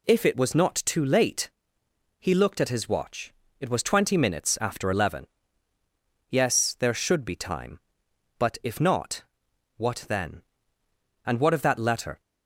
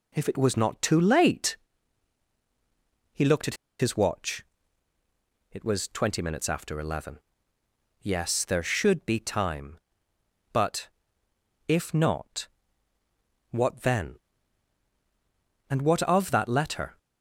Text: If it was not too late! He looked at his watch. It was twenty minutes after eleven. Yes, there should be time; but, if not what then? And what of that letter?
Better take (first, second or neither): first